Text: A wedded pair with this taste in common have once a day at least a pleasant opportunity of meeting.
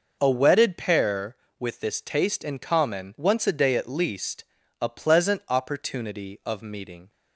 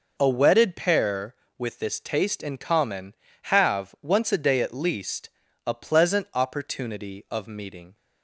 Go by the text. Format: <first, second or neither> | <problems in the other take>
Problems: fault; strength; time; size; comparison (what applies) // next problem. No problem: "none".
second | skips "have"; at 3.1 s // pauses between "least" and "a"; at 4.4 s; 0.40 s long; also in the second